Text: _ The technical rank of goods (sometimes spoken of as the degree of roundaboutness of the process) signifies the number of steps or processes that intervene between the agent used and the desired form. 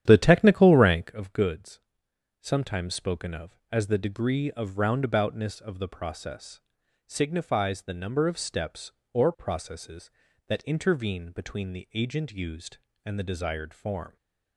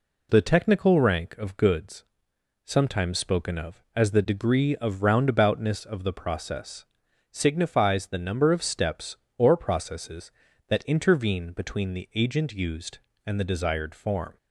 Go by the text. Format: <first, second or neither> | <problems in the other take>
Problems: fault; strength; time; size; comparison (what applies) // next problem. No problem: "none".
second | starts louder than the rest; strong; until 1.2 s; 10.5 dB